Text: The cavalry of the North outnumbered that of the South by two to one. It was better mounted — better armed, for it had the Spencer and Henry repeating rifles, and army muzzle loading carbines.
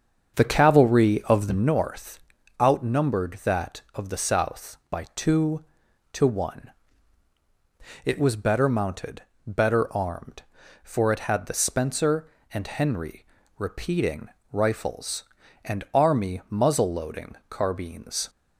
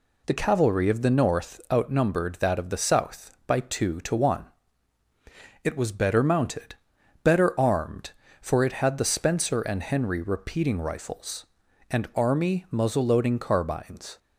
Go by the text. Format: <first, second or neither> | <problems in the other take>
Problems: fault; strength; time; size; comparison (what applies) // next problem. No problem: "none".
second | starts louder than the rest; until 1.9 s; 7 dB // pauses between "North" and "outnumbered"; at 2.1 s; 0.42 s long // pauses between "Henry" and "repeating"; slight; at 13.2 s; 0.34 s long // pauses between "repeating" and "rifles"; slight; at 14.2 s; 0.24 s long